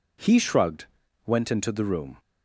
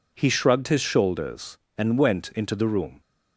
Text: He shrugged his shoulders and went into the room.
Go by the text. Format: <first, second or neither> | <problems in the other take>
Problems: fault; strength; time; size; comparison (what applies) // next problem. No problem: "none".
second | skips "his shoulders and"; at 1.0 s